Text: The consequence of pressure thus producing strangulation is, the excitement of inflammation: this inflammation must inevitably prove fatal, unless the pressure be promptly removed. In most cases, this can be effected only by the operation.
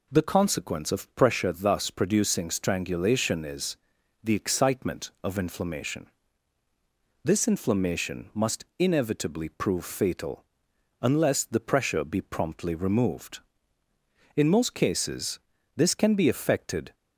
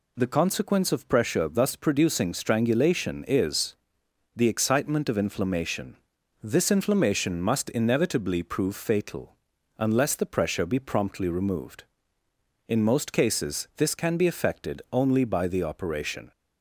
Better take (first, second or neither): second